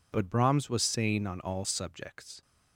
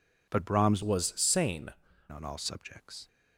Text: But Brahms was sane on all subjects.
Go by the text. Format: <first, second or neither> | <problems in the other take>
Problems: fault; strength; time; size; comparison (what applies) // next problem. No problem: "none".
first | changes voice from "was" to "sane"; from 0.8 to 1.6 s; 0.8 s long